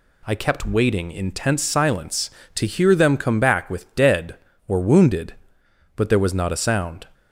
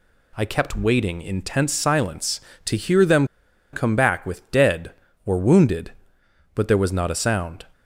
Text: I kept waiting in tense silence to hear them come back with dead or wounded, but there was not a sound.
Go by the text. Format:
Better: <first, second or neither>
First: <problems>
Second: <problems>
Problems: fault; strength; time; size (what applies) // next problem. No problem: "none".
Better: first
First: none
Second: pauses between "them" and "come"; noticeable; at 3.2 s; 0.46 s long